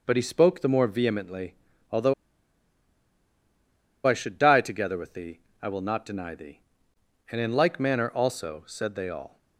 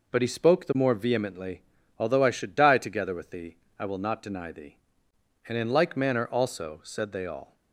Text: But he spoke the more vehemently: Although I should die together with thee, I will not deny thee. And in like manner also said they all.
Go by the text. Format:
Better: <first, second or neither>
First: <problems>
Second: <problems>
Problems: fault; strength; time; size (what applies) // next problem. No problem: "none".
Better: second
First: pauses between "Although" and "I"; strong; at 2.1 s; 1.9 s long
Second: none